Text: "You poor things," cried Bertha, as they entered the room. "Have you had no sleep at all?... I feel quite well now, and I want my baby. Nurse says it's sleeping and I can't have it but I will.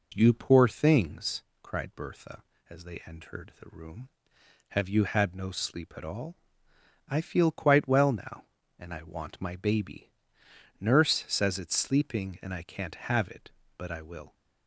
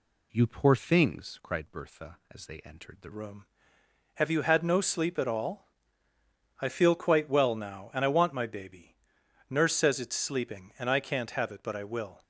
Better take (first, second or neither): first